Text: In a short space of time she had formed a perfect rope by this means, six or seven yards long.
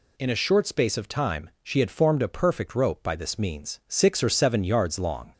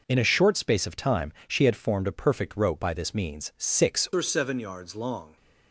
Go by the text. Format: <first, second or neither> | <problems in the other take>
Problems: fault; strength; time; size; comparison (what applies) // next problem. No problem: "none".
first | pauses between "time" and "she"; slight; at 1.3 s; 0.16 s long // changes voice at "or"; from 4.1 s on; 1.2 s long